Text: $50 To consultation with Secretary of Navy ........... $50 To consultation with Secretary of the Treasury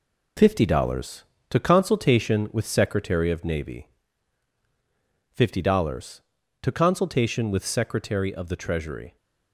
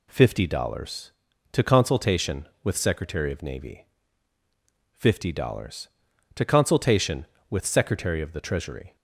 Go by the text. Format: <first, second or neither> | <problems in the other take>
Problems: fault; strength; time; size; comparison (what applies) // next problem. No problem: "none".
second | gets quieter; noticeable; throughout; 6 dB